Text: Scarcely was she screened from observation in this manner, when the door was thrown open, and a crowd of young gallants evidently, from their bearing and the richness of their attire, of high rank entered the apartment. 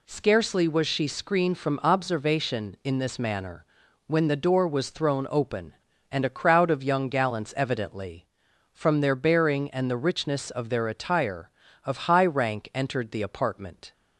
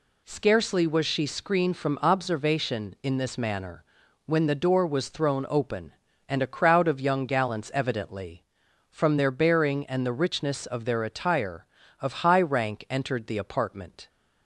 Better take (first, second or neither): neither